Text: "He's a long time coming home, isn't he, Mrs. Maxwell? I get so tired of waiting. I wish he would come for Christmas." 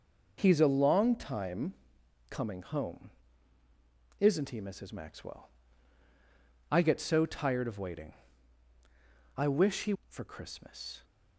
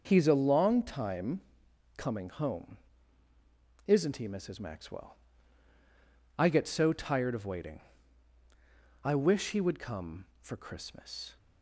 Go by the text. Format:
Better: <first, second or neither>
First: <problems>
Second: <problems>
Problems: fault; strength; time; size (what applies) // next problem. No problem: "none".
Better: second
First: pauses between "time" and "coming"; noticeable; at 1.7 s; 0.56 s long // skips "would come"; at 10.0 s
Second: pauses between "time" and "coming"; noticeable; at 1.4 s; 0.56 s long